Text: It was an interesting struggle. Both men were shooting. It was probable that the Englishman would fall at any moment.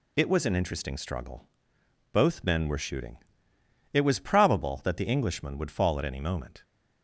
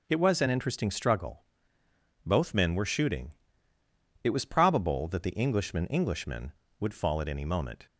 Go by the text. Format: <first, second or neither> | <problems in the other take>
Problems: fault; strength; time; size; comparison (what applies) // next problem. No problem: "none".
first | says "Englishman" twice; at 5.8 s